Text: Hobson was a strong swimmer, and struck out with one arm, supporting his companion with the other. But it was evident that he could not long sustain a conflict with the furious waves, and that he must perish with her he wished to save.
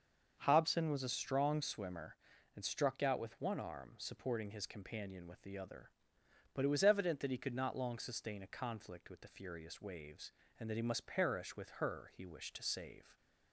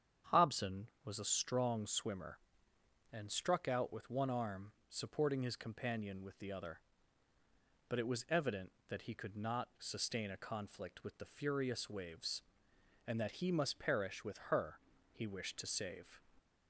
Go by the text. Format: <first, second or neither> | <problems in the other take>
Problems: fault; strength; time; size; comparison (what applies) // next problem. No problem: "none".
first | starts louder than the rest; strong; until 1.4 s; 8 dB; also in the first // skips "long"; at 9.7 s // pauses between "her" and "he"; slight; at 14.7 s; 0.32 s long